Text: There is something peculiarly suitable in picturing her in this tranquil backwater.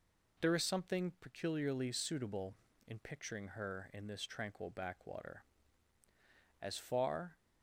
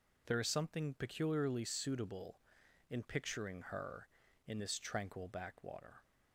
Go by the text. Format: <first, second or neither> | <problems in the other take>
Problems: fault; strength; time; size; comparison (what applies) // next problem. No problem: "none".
second | goes on to say "As far"; noticeable; from 6.6 s on; 0.76 s long